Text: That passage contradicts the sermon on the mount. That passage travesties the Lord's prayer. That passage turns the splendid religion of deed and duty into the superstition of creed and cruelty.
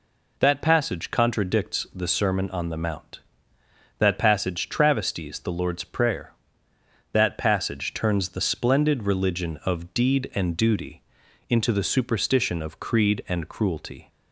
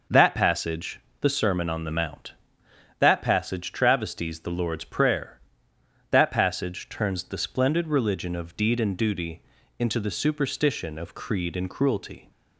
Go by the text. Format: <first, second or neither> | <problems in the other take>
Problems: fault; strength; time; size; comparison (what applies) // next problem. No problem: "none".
first | skips "contradicts"; at 1.0 s // pauses between "duty" and "into"; slight; at 9.4 s; 0.36 s long; noticeable in the first